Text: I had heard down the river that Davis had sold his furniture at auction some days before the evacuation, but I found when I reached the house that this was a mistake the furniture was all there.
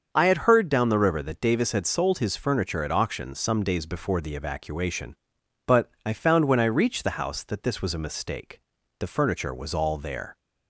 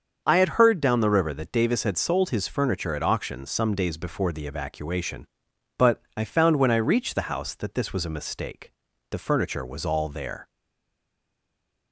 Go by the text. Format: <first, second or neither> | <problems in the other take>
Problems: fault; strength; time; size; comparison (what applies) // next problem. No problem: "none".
first | starts louder than the rest; until 1.2 s; 6.5 dB; also in the first // pauses between "but" and "I"; slight; at 6.0 s; 0.16 s long; slight in the first // pauses between "mistake" and "the"; at 8.7 s; 0.40 s long; also in the first // stays silent after the last word; noticeable; from 10.4 s on; 1.5 s long